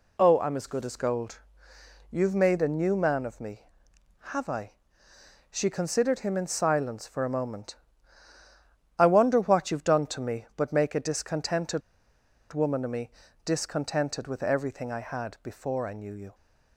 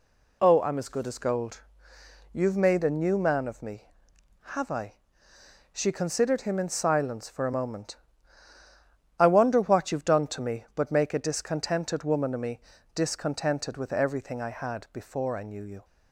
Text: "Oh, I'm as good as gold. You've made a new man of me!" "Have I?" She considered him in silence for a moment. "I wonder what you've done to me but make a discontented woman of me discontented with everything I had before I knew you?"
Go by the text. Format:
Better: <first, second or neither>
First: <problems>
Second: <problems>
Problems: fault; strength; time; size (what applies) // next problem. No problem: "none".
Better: second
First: pauses between "discontented" and "woman"; noticeable; at 11.8 s; 0.71 s long // pauses between "me" and "discontented"; slight; at 13.1 s; 0.34 s long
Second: pauses between "me" and "discontented"; slight; at 12.6 s; 0.34 s long